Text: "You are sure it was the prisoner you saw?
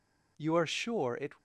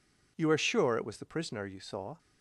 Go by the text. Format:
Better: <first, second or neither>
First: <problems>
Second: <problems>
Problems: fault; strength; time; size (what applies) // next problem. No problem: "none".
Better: second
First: stops before "was the prisoner you saw"; at 1.3 s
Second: none